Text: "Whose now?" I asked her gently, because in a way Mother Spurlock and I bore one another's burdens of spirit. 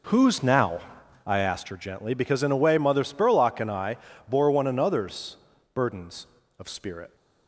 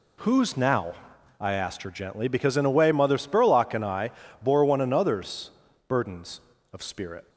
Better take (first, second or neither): second